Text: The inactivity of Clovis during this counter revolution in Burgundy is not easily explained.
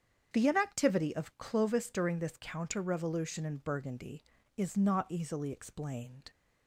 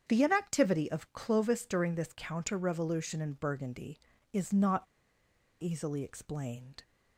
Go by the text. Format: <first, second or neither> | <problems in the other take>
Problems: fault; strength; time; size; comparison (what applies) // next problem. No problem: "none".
first | starts louder than the rest; strong; until 1.0 s; 8 dB; strong in the first // pauses between "not" and "easily"; noticeable; at 4.8 s; 0.78 s long